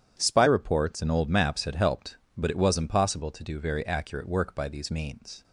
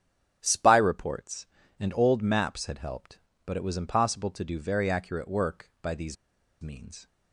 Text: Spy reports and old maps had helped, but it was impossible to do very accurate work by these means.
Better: first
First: starts louder than the rest; strong; until 1.2 s; 9.5 dB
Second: starts louder than the rest; strong; until 1.4 s; 10.5 dB // pauses between "these" and "means"; at 6.1 s; 0.45 s long

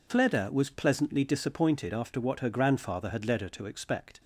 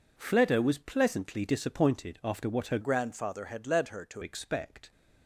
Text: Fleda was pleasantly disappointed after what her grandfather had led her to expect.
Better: first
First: none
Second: changes voice from "grandfather" to "to"; from 2.8 to 4.2 s; 1.4 s long

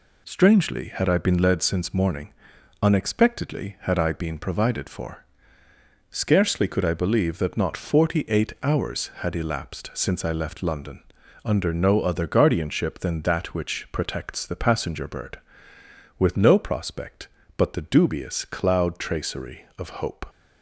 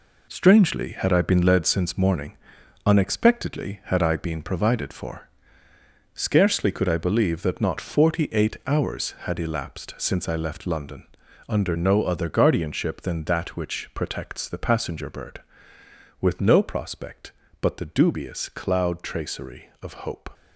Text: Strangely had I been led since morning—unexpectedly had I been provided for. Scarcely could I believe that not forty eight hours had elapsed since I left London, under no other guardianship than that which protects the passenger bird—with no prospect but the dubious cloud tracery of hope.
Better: first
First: none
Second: gets quieter; strong; throughout; 8 dB

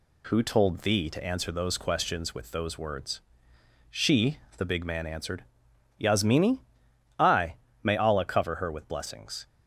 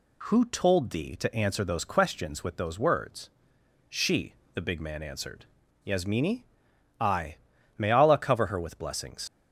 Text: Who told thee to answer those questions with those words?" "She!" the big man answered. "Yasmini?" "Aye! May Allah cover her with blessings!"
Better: first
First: none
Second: leaves "blessings" unfinished; at 9.2 s; 120 ms

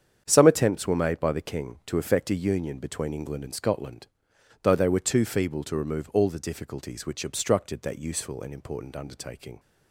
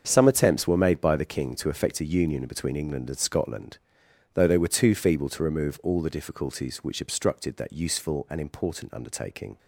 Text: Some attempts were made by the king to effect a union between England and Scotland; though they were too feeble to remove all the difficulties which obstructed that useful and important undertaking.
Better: neither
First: starts louder than the rest; strong; until 1.2 s; 8 dB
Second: starts louder than the rest; until 1.0 s; 7 dB

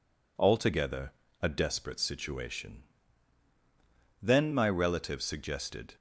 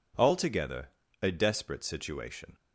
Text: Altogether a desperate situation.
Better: second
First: pauses between "Altogether" and "a"; slight; at 1.1 s; 0.30 s long // goes on to say "Then my relative suggested"; strong; from 4.2 s on; 1.6 s long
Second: pauses between "Altogether" and "a"; at 0.8 s; 0.37 s long

